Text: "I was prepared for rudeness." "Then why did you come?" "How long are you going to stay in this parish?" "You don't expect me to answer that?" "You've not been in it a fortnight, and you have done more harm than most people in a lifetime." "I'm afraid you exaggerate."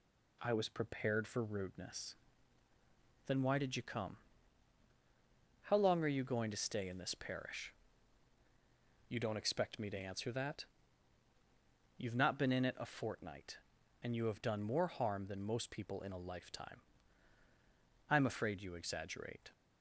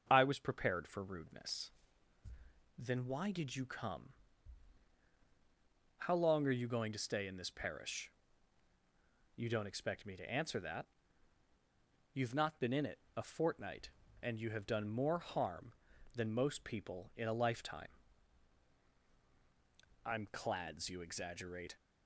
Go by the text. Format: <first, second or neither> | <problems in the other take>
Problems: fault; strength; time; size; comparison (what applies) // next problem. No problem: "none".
first | starts louder than the rest; until 1.1 s; 6.5 dB // pauses between "it" and "a"; slight; at 12.9 s; 0.18 s long // says "clads" for "afraid"; at 20.2 s